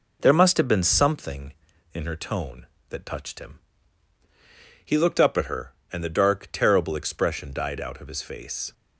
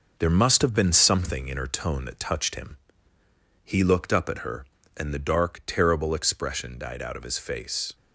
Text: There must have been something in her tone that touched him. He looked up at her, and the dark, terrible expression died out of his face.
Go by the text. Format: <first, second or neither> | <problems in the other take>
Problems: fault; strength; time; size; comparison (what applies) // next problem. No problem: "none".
first | gets quieter; noticeable; throughout; 5 dB